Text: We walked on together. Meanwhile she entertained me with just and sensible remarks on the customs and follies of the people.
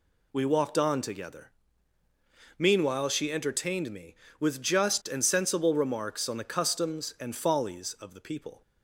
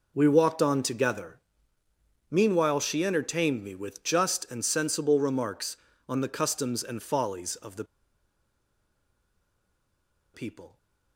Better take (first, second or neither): first